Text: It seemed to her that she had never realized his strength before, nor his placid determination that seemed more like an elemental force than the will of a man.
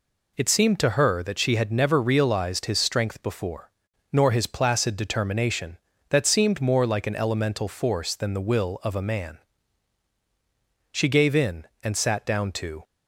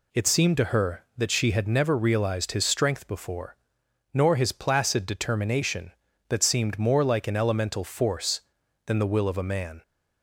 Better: second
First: goes on to say "She gave in and sat down to"; strong; from 10.9 s on; 1.9 s long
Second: none

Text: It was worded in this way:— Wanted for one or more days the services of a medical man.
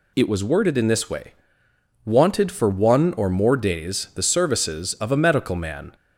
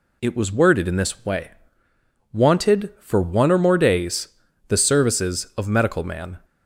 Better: first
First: none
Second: pauses between "days" and "the"; at 4.2 s; 0.40 s long // skips "a"; at 5.6 s

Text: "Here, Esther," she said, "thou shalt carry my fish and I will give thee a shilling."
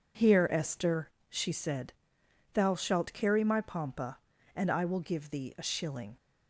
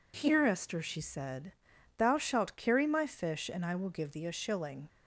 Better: second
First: says "pompa" for "fish"; at 3.5 s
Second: none

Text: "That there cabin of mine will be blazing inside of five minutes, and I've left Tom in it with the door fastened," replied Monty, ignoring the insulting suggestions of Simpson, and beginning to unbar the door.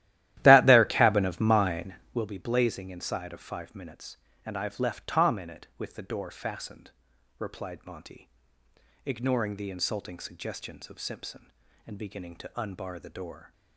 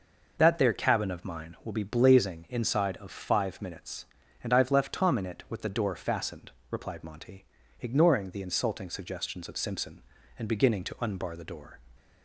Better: second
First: starts louder than the rest; strong; until 2.3 s; 14 dB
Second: none

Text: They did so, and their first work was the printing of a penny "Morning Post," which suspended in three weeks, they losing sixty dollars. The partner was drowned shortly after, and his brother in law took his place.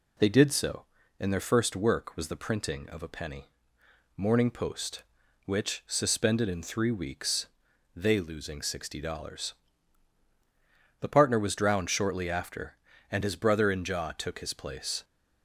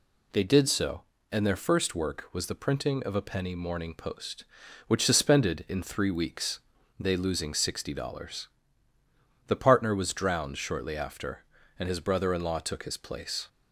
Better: second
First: pauses between "penny" and "Morning"; noticeable; at 3.5 s; 0.64 s long // says "jaw" for "law"; at 13.8 s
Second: none

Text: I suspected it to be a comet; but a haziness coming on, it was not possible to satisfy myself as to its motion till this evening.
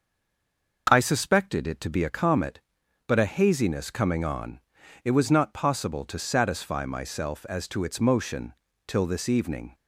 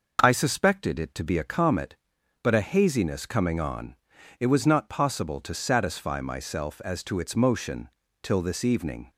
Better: second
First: stays silent before the first word; slight; until 0.8 s; 0.8 s long // pauses between "motion" and "till"; slight; at 8.5 s; 0.34 s long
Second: pauses between "motion" and "till"; slight; at 7.8 s; 0.34 s long

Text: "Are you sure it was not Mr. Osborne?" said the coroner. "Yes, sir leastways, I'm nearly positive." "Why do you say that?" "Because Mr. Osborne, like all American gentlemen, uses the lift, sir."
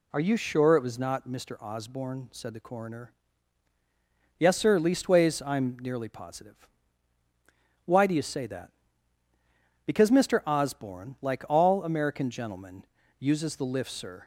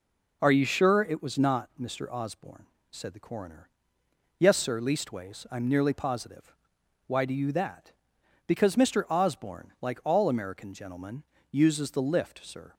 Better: first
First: none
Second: skips "say"; at 7.5 s

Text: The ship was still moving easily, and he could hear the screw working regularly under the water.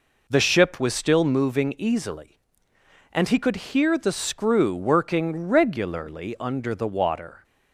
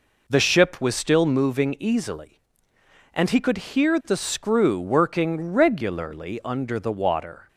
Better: neither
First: none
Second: none

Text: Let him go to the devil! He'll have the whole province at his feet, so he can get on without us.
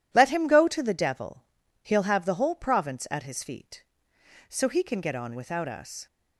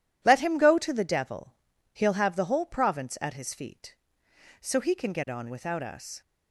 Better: neither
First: none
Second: none

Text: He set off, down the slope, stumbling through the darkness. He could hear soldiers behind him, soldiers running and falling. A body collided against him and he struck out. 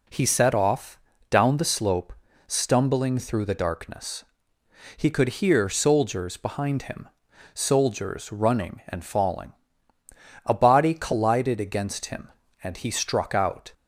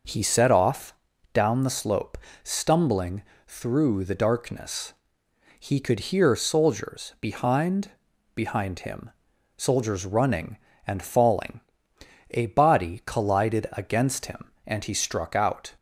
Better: first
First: none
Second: pauses between "stumbling" and "through"; slight; at 3.2 s; 0.24 s long // says "behind" twice; at 8.3 s

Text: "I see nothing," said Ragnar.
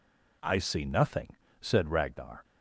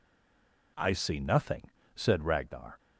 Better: first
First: none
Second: stays silent before the first word; slight; until 0.7 s; 0.7 s long

